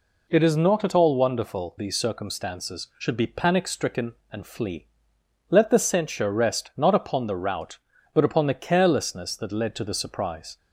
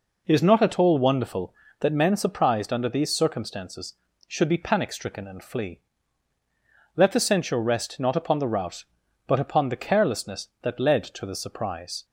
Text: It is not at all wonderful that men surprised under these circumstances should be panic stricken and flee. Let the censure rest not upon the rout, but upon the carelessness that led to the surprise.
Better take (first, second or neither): second